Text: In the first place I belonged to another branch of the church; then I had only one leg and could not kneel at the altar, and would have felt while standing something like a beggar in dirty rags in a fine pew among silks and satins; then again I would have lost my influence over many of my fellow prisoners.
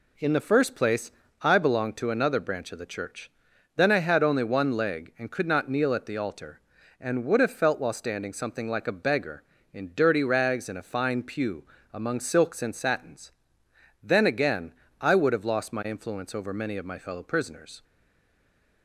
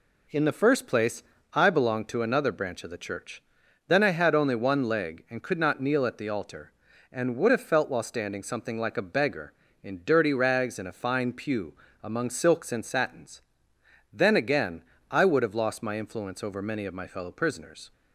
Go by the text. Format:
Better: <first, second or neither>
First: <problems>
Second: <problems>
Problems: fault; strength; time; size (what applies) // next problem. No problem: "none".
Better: second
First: pauses between "place" and "I"; slight; at 1.1 s; 0.30 s long // pauses between "pew" and "among"; slight; at 11.6 s; 0.28 s long // pauses between "again" and "I"; slight; at 14.7 s; 0.30 s long // stays silent after the last word; from 17.8 s on; 1.0 s long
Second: pauses between "place" and "I"; slight; at 1.2 s; 0.30 s long // pauses between "pew" and "among"; slight; at 11.7 s; 0.28 s long // pauses between "again" and "I"; slight; at 14.8 s; 0.30 s long